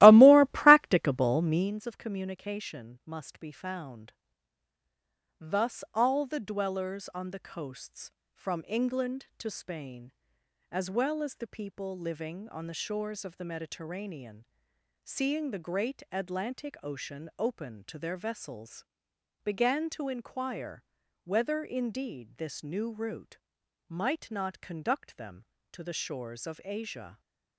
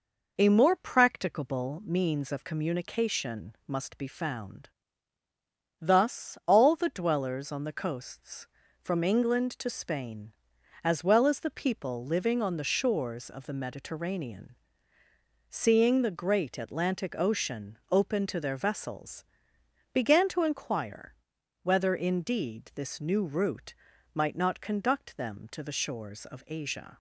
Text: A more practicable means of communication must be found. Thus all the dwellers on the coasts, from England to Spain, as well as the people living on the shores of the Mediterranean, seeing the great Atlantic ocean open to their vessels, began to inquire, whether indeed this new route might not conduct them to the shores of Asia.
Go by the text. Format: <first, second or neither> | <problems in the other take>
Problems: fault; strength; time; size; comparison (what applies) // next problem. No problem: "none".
second | starts louder than the rest; strong; until 1.7 s; 16 dB // pauses between "route" and "might"; noticeable; at 23.3 s; 0.50 s long; also in the second